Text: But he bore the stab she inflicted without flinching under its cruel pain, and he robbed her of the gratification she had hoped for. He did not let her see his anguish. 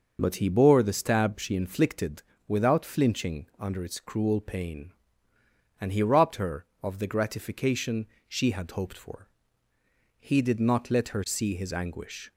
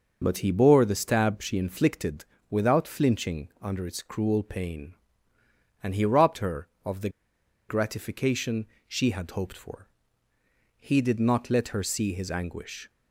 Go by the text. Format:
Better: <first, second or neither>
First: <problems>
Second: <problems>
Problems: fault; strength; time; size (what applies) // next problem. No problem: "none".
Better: first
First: pauses between "inflicted" and "without"; slight; at 2.2 s; 0.24 s long // pauses between "gratification" and "she"; slight; at 8.0 s; 0.22 s long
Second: pauses between "inflicted" and "without"; slight; at 2.2 s; 0.24 s long // pauses between "the" and "gratification"; noticeable; at 7.0 s; 0.60 s long // pauses between "gratification" and "she"; slight; at 8.6 s; 0.22 s long